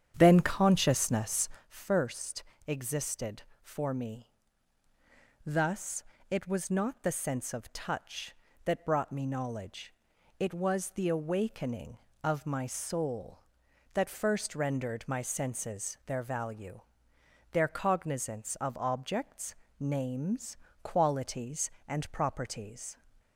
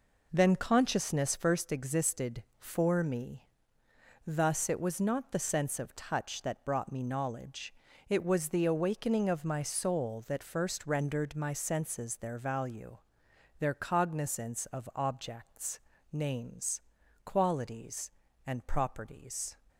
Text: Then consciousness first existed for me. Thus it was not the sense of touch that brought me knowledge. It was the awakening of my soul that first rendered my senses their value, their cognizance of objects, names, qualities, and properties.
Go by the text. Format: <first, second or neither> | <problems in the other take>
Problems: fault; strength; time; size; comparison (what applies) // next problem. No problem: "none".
second | starts louder than the rest; strong; until 1.7 s; 9 dB // pauses between "consciousness" and "first"; slight; at 1.4 s; 0.18 s long // pauses between "first" and "existed"; slight; at 2.4 s; 0.24 s long // pauses between "Thus" and "it"; slight; at 6.0 s; 0.28 s long